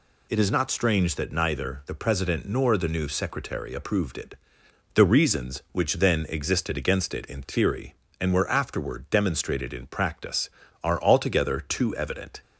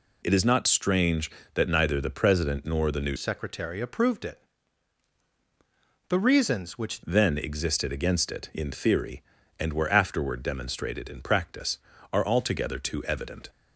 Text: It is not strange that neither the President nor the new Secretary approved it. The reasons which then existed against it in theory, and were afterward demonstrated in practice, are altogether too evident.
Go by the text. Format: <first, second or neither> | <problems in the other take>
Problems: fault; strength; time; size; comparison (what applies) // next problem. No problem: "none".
first | changes voice from "Secretary" to "which"; from 3.1 to 7.0 s; 3.9 s long